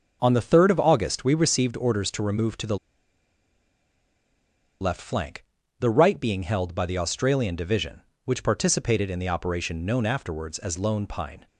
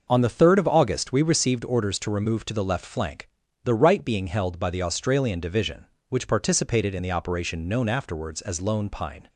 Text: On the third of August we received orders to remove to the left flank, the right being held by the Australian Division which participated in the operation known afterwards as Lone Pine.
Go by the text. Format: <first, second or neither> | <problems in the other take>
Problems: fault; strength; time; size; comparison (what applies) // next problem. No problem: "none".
second | pauses between "the" and "left"; strong; at 2.7 s; 2.0 s long